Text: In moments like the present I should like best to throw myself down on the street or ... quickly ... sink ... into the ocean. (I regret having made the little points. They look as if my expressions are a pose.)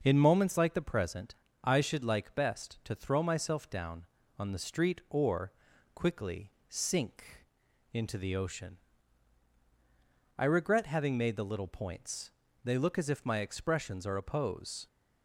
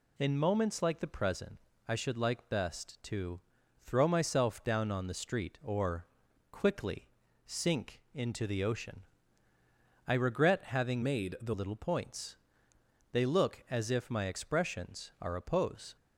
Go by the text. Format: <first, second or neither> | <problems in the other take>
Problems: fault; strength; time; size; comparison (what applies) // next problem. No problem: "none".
first | pauses between "present" and "I"; slight; at 1.5 s; 0.30 s long; slight in the first // pauses between "to" and "throw"; at 3.4 s; 0.44 s long // changes voice from "made" to "the"; from 11.0 to 11.5 s; 0.5 s long